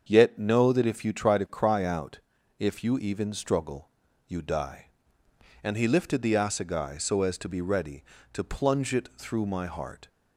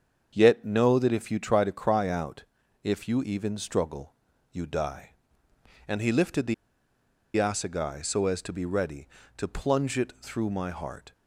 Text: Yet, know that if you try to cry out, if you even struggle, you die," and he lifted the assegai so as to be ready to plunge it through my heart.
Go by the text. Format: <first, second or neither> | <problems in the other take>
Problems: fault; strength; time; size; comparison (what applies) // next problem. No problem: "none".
first | starts louder than the rest; until 1.3 s; 7 dB; also in the first // pauses between "the" and "assegai"; noticeable; at 6.5 s; 0.81 s long